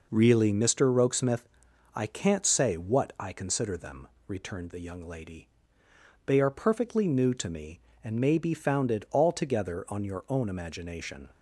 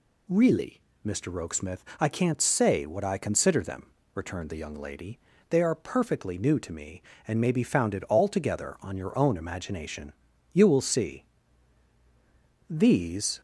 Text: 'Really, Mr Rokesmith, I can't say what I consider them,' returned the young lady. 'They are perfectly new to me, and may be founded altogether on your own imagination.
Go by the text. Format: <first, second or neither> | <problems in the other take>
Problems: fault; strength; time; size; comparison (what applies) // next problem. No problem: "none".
first | goes on to say "You will see These"; strong; from 10.5 s on; 2.8 s long